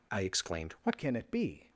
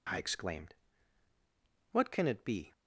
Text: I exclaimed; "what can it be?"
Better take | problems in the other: second | changes voice at "can"; from 0.9 s on; 0.7 s long

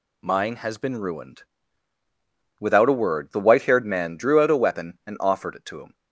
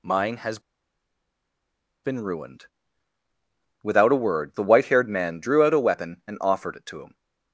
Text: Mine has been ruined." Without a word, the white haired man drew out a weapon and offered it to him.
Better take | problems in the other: first | pauses between "has" and "been"; strong; at 0.5 s; 1.4 s long

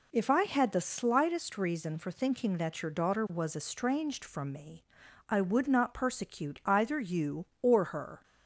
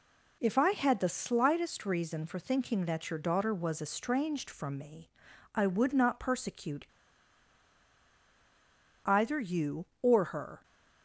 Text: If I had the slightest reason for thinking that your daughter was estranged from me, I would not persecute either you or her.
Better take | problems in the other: first | pauses between "persecute" and "either"; strong; at 6.8 s; 2.2 s long

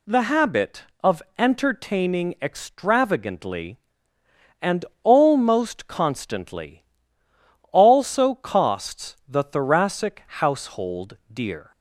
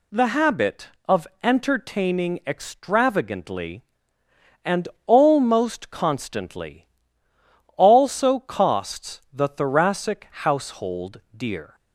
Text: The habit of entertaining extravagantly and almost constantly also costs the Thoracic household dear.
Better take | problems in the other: neither | pauses between "of" and "entertaining"; slight; the same in both // pauses between "and" and "almost"; slight; the same in both // pauses between "constantly" and "also"; noticeable; the same in both

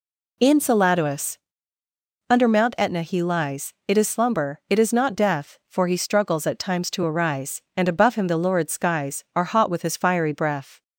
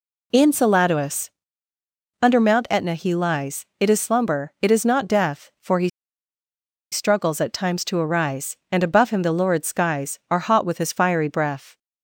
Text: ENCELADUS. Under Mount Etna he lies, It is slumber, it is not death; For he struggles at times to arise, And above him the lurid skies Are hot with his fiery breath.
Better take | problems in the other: first | pauses between "he" and "struggles"; at 5.8 s; 1.0 s long

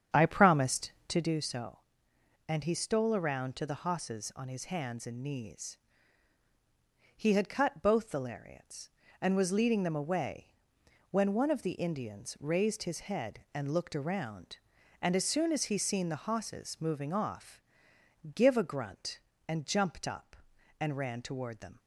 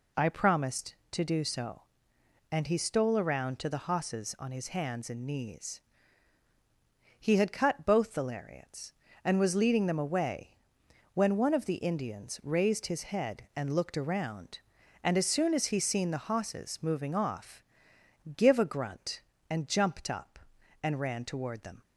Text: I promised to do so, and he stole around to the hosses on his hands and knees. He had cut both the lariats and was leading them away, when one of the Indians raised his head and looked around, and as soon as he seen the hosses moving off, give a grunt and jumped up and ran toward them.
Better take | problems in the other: second | starts louder than the rest; strong; until 1.4 s; 8.5 dB

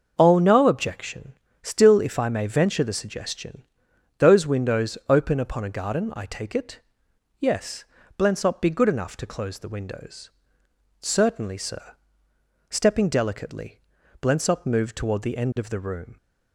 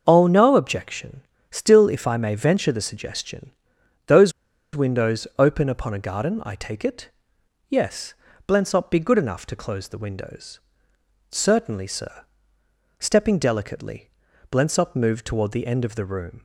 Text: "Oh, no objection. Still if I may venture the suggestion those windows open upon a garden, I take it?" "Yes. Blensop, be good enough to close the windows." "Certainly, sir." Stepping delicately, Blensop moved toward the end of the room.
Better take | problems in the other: first | starts louder than the rest; until 1.0 s; 6.5 dB; also in the first // pauses between "suggestion" and "those"; noticeable; at 3.5 s; 0.56 s long; noticeable in the first // pauses between "those" and "windows"; at 4.3 s; 0.44 s long

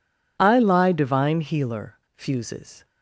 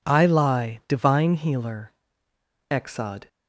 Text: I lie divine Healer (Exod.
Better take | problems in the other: second | says "Fuses" for "Exod"; at 2.1 s

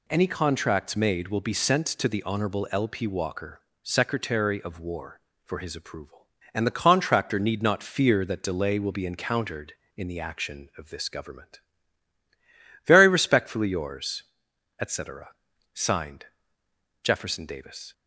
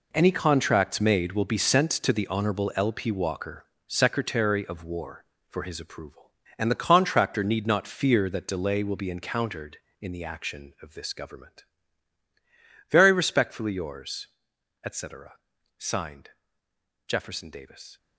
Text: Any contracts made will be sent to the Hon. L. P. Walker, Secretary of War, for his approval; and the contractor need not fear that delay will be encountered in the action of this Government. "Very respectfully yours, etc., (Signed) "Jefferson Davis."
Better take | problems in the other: first | gets quieter; strong; throughout; 12 dB

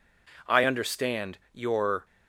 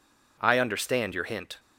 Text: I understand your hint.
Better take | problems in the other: second | pauses between "understand" and "your"; slight; at 1.3 s; 0.15 s long // stops before "hint"; at 2.0 s

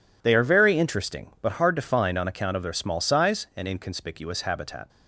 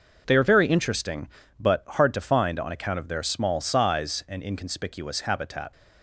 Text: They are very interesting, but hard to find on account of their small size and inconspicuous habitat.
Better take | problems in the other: neither | none

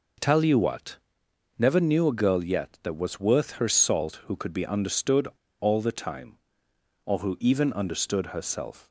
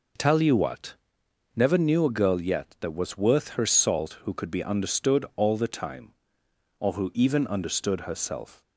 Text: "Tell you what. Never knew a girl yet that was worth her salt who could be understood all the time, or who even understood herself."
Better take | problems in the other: second | pauses between "understood" and "all"; slight; at 5.2 s; 0.31 s long

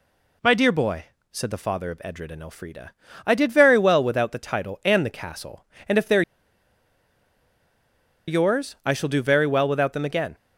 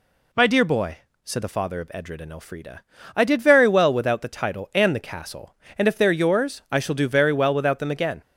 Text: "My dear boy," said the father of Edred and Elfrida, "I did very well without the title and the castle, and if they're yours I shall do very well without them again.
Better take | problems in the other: second | pauses between "they're" and "yours"; strong; at 6.2 s; 2.0 s long

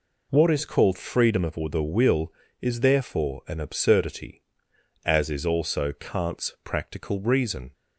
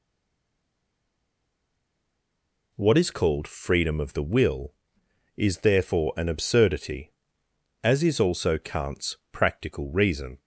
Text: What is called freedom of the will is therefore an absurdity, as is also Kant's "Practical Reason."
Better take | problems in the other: first | stays silent before the first word; strong; until 2.7 s; 2.7 s long

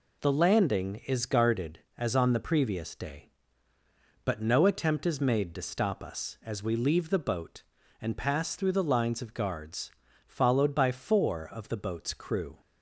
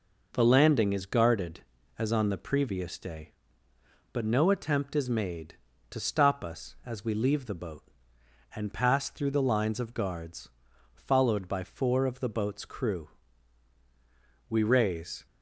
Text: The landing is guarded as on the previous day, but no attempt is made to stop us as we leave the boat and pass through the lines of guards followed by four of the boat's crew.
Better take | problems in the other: first | pauses between "guards" and "followed"; at 10.4 s; 0.44 s long; slight in the first // goes on to say "We raise"; noticeable; from 14.4 s on; 0.78 s long

